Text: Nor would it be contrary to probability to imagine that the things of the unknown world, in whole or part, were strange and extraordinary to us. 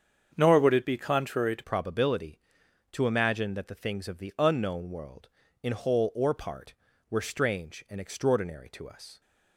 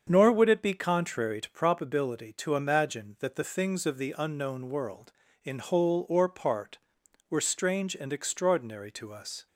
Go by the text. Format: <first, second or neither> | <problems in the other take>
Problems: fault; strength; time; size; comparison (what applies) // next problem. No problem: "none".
second | starts louder than the rest; strong; until 1.3 s; 7 dB; strong in the second // changes voice at "probability"; from 1.6 s on; 7.6 s long